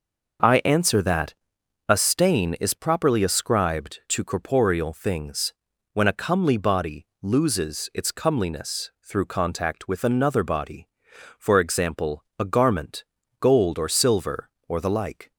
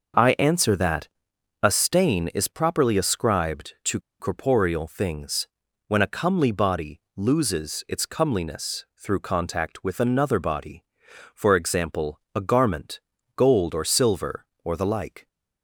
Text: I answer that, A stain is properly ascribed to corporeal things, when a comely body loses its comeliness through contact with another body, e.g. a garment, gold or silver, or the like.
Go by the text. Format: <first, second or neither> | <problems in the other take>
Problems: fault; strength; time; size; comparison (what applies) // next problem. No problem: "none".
first | pauses between "to" and "corporeal"; slight; at 3.9 s; 0.20 s long // pauses between "body" and "loses"; slight; at 6.9 s; 0.16 s long; slight in the first